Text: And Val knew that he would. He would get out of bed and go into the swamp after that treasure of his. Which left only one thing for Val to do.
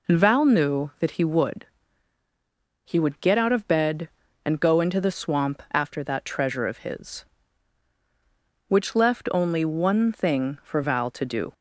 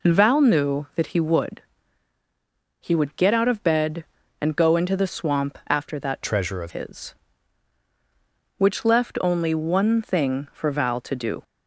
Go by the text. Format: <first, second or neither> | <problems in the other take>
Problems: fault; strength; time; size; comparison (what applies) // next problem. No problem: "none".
first | changes voice from "treasure" to "of"; from 6.2 to 6.7 s; 0.5 s long